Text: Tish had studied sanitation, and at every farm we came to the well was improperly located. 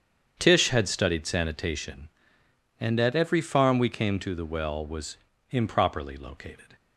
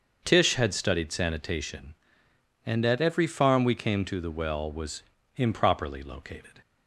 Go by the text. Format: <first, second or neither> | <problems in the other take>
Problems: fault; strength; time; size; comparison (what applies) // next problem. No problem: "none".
second | gets quieter; strong; throughout; 13 dB // starts louder than the rest; strong; until 1.3 s; 8 dB; also in the second // pauses between "was" and "improperly"; slight; at 5.1 s; 0.34 s long; slight in the second